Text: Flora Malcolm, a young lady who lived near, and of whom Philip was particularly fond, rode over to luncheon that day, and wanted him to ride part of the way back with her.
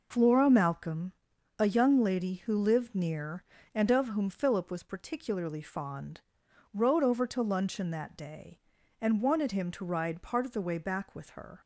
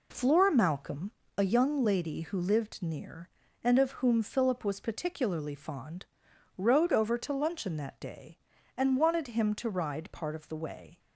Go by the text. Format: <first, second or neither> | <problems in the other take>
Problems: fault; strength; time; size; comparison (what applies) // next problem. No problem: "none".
first | stops before "back with her"; at 10.9 s